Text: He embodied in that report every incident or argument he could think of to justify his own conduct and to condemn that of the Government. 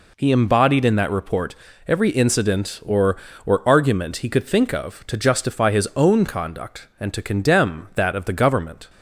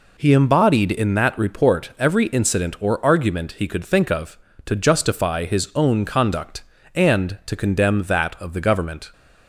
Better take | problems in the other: second | pauses between "report" and "every"; slight; at 1.5 s; 0.32 s long // says "or" twice; at 3.4 s

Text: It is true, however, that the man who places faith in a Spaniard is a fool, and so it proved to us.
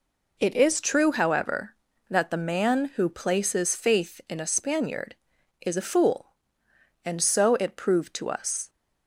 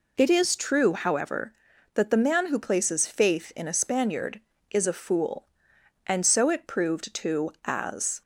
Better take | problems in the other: first | says "as" for "us"; at 7.6 s

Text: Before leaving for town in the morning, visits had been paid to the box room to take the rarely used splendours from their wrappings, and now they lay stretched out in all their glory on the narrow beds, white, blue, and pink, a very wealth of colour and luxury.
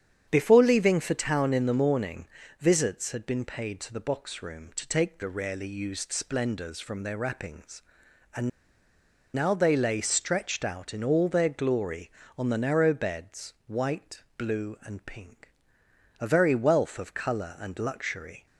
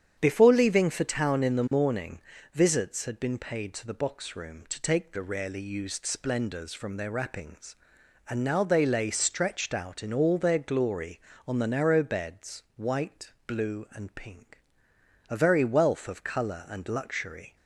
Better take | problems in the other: second | starts louder than the rest; strong; until 1.3 s; 8.5 dB; strong in the second // pauses between "and" and "now"; noticeable; at 8.4 s; 0.84 s long

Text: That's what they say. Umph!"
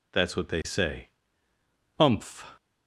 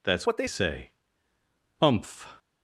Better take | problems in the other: first | changes voice from "what" to "they"; from 0.2 to 0.4 s; 0.2 s long

